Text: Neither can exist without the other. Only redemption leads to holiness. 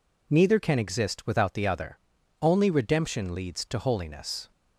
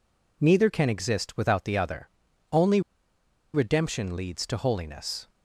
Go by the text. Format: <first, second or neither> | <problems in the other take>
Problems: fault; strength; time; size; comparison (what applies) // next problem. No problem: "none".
first | pauses between "Only" and "redemption"; noticeable; at 2.7 s; 0.73 s long